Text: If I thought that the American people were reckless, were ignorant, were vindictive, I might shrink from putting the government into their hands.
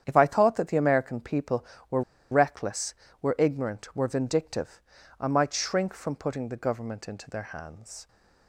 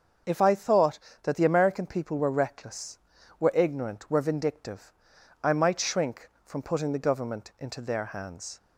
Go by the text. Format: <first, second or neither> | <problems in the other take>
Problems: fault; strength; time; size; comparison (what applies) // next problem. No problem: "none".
second | starts louder than the rest; strong; until 1.0 s; 8.5 dB; also in the second // pauses between "were" and "reckless"; slight; at 2.0 s; 0.29 s long